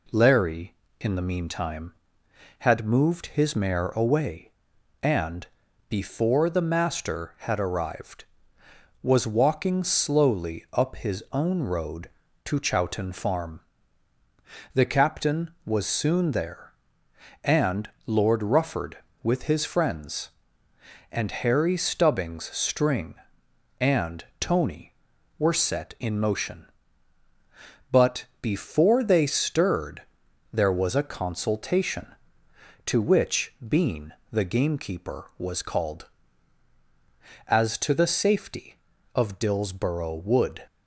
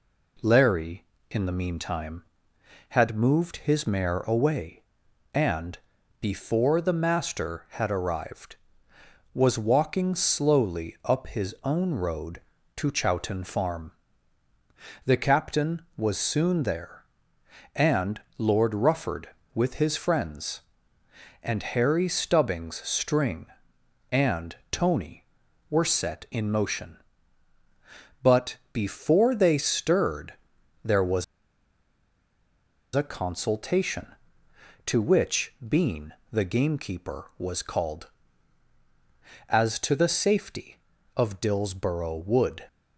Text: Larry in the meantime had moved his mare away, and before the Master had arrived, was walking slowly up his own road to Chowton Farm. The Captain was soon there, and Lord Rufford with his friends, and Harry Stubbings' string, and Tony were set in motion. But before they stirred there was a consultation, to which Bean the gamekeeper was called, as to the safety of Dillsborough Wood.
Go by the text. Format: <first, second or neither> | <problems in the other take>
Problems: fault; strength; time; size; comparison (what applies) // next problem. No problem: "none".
first | pauses between "and" and "before"; at 5.7 s; 0.42 s long; also in the first // pauses between "and" and "Lord"; slight; at 18.2 s; 0.16 s long; slight in the first // pauses between "and" and "Tony"; slight; at 24.5 s; 0.16 s long; slight in the first // pauses between "But" and "before"; slight; at 28.5 s; 0.16 s long; slight in the first // pauses between "stirred" and "there"; noticeable; at 30.3 s; 0.50 s long; noticeable in the first // pauses between "was" and "a"; strong; at 31.2 s; 1.7 s long // pauses between "Bean" and "the"; slight; at 36.1 s; 0.18 s long; slight in the first